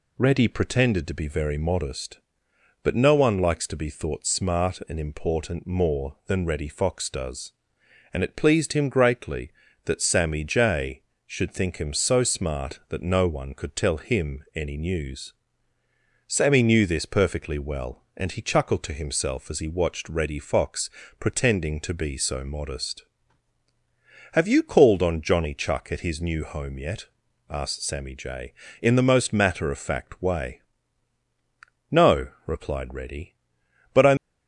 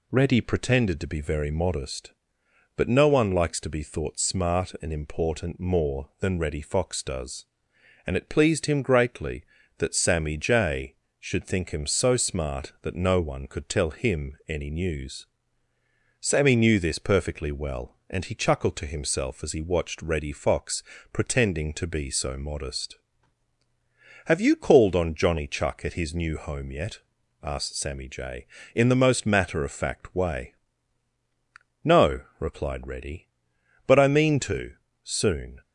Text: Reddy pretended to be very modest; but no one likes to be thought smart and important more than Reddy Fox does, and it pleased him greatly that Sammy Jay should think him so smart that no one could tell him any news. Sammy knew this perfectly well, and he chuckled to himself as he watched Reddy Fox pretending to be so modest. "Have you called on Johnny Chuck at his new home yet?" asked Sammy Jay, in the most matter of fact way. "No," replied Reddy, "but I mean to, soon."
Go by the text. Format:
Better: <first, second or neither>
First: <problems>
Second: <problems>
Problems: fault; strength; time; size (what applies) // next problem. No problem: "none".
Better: second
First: pauses between "Fox" and "pretending"; slight; at 20.8 s; 0.32 s long // stops before "mean to soon"; at 34.1 s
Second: pauses between "Fox" and "pretending"; slight; at 20.8 s; 0.32 s long